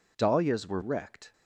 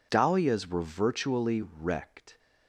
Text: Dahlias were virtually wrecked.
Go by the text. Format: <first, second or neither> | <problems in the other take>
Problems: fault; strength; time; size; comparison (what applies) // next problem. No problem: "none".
second | skips "virtually"; at 0.8 s